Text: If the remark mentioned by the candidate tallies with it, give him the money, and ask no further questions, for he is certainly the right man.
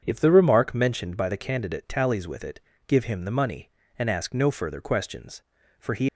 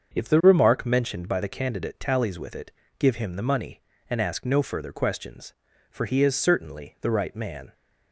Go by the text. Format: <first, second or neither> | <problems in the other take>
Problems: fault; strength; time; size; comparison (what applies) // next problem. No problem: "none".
second | starts louder than the rest; strong; until 1.0 s; 7 dB; also in the second // stops before "is certainly the right man"; at 6.0 s